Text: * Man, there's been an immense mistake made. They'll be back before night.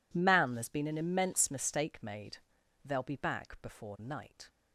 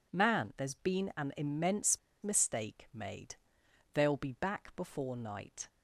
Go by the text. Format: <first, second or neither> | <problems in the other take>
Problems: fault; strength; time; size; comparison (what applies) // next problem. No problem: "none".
first | pauses between "immense" and "mistake"; slight; at 1.9 s; 0.25 s long